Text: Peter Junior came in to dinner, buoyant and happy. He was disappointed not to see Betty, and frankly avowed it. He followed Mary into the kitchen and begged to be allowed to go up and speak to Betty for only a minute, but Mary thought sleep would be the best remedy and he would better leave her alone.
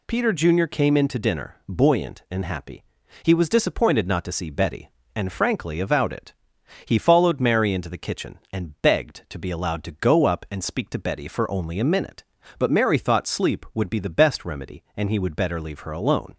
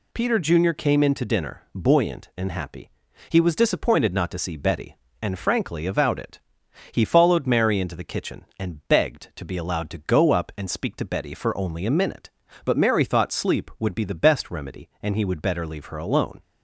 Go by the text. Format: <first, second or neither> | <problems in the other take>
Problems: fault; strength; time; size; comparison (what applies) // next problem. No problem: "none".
neither | none